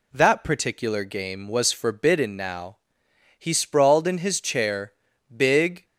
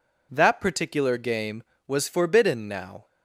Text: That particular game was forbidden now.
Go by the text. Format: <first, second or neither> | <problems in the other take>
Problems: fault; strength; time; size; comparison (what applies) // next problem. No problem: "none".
second | goes on to say "He sprawled in his chair big"; strong; from 3.3 s on; 2.4 s long